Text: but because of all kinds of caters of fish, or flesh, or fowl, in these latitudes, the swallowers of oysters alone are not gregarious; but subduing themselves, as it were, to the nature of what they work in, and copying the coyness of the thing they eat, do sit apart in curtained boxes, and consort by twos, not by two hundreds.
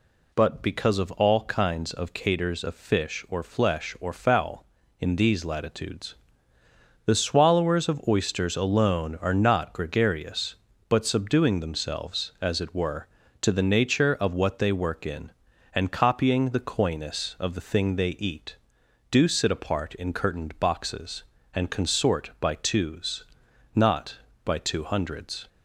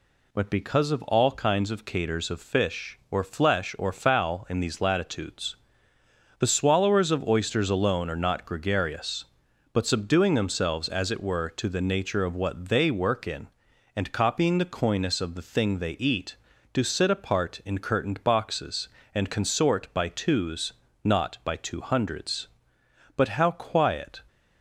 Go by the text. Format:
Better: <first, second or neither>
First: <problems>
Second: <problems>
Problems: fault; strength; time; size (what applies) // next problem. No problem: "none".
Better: first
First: none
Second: goes on to say "But how quiet"; noticeable; from 23.1 s on; 1.0 s long